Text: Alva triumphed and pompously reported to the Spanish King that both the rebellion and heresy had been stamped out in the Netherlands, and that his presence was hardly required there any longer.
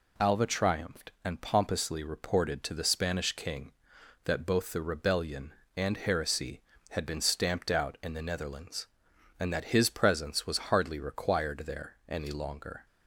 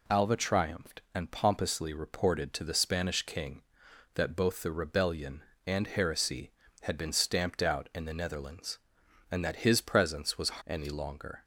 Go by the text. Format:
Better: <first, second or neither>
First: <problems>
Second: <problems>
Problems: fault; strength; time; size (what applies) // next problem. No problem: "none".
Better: first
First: none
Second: skips "hardly required there"; at 10.6 s